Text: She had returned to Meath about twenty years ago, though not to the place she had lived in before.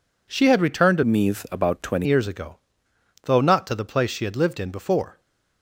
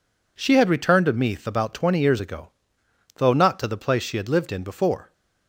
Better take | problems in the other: second | changes voice from "Meath" to "twenty"; from 1.0 to 2.0 s; 1.0 s long

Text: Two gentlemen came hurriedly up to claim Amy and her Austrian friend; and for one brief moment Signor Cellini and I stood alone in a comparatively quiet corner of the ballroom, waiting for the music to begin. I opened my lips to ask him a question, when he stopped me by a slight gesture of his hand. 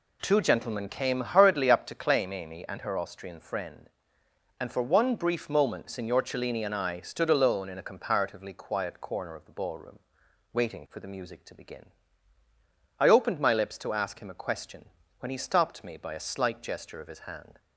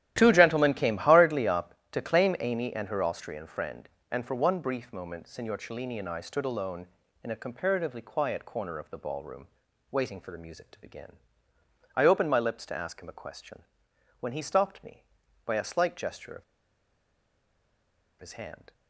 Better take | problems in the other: first | starts louder than the rest; strong; until 1.1 s; 12.5 dB // pauses between "of" and "his"; strong; at 16.4 s; 1.7 s long

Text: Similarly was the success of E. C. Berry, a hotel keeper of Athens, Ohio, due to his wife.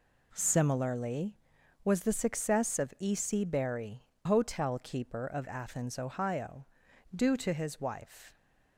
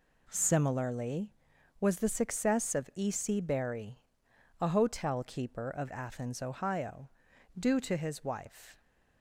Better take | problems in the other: second | skips "a"; at 4.1 s

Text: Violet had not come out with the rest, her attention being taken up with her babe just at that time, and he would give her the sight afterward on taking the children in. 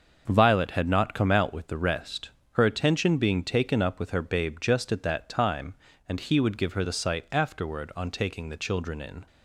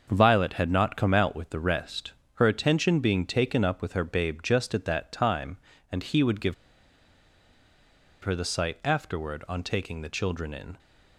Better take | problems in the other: first | starts louder than the rest; until 1.1 s; 6.5 dB; also in the first // pauses between "give" and "her"; strong; at 6.5 s; 1.6 s long

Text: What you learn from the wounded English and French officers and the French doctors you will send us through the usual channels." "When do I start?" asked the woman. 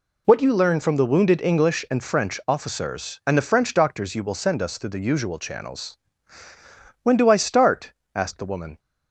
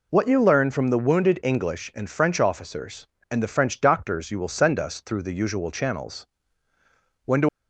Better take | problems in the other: first | stops before "I start asked the woman"; at 7.4 s

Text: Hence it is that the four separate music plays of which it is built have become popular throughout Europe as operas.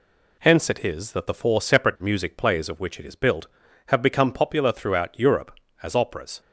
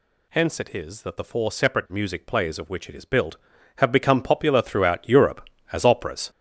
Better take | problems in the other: first | gets louder; strong; throughout; 9 dB

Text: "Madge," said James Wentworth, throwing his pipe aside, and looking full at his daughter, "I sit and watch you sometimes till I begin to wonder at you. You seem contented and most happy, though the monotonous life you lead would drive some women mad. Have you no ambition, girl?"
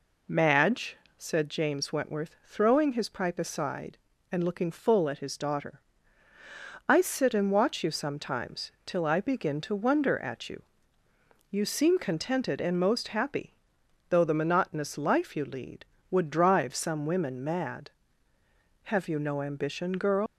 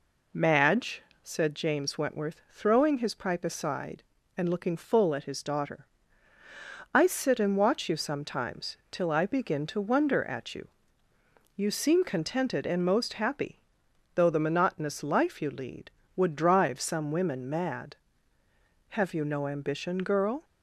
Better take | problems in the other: second | leaves "girl" unfinished; at 20.2 s; 120 ms

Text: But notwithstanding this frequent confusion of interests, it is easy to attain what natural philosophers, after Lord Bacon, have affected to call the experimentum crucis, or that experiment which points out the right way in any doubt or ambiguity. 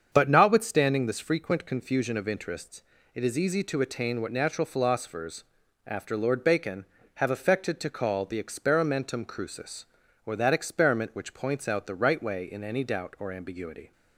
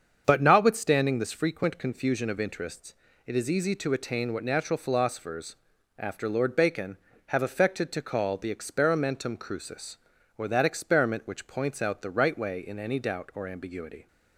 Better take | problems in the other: neither | starts louder than the rest; strong; the same in both

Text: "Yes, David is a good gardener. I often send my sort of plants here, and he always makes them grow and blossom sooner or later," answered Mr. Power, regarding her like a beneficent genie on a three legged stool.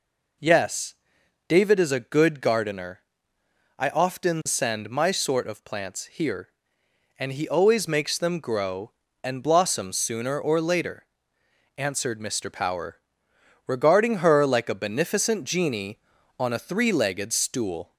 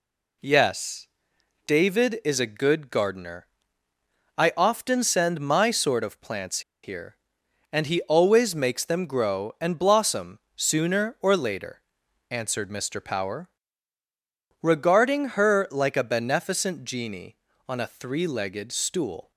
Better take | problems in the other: first | pauses between "plants" and "here"; slight; at 6.6 s; 0.22 s long // pauses between "blossom" and "sooner"; slight; at 10.4 s; 0.16 s long

